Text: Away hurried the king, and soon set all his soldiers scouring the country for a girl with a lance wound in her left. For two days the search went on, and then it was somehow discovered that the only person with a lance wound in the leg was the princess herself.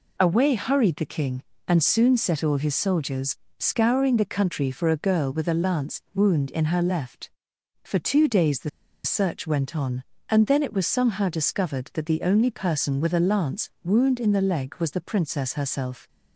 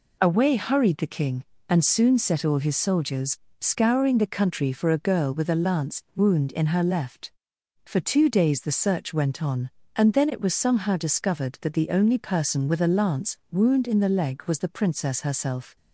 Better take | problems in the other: second | pauses between "soldiers" and "scouring"; slight; at 3.3 s; 0.22 s long; slight in the second // pauses between "the" and "search"; slight; at 8.6 s; 0.35 s long

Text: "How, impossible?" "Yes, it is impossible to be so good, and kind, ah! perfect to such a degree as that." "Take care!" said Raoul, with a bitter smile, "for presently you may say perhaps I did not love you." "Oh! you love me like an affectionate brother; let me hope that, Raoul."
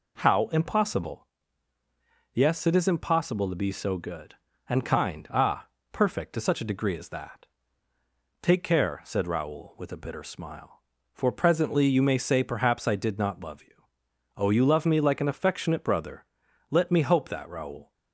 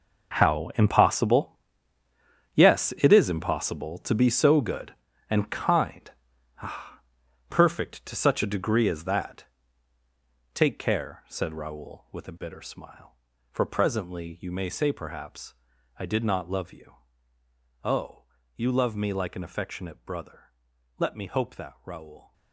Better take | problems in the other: first | gets quieter; strong; throughout; 12.5 dB // pauses between "perhaps" and "I"; at 15.5 s; 0.42 s long

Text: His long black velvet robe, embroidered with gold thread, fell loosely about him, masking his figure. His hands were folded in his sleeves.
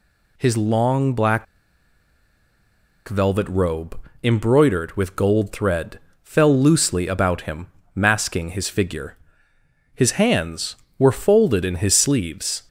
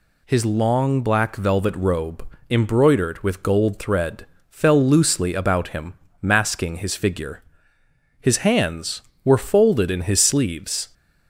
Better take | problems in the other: second | pauses between "black" and "velvet"; strong; at 1.4 s; 1.6 s long

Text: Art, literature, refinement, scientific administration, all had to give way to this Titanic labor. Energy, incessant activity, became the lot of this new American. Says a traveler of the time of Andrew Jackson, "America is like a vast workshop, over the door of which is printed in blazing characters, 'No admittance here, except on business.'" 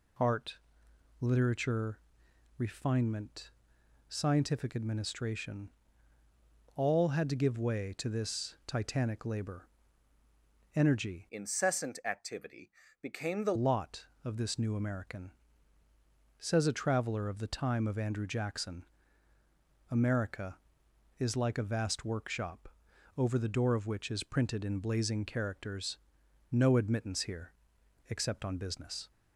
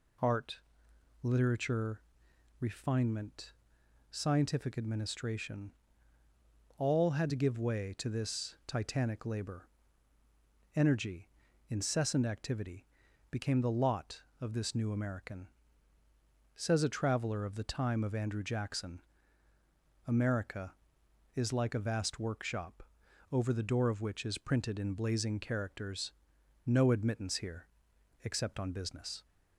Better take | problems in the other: second | changes voice from "incessant" to "the"; from 11.3 to 13.5 s; 2.2 s long

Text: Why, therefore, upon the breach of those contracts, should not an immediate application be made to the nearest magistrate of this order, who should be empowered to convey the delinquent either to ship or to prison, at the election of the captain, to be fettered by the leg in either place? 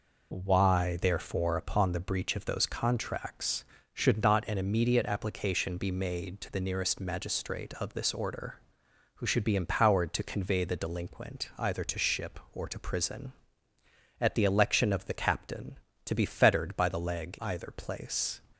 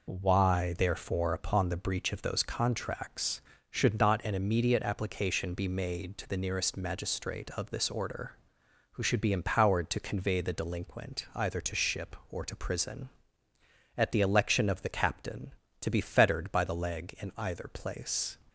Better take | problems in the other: second | skips "in"; at 17.3 s

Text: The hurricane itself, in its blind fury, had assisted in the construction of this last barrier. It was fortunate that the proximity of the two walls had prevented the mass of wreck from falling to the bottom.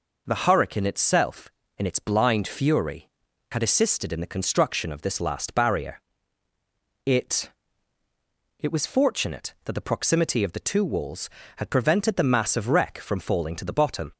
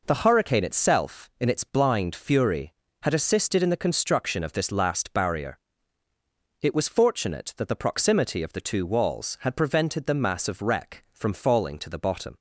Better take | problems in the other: second | says "It" twice; at 8.5 s

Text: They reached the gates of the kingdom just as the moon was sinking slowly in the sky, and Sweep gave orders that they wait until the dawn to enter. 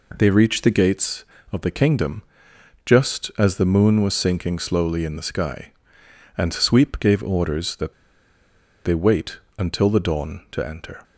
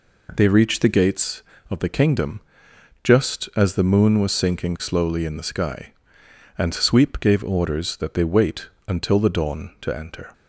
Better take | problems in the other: second | pauses between "kingdom" and "just"; noticeable; at 2.2 s; 0.62 s long; noticeable in the second // pauses between "that" and "they"; noticeable; at 7.9 s; 0.91 s long // pauses between "wait" and "until"; slight; at 9.3 s; 0.18 s long; slight in the second

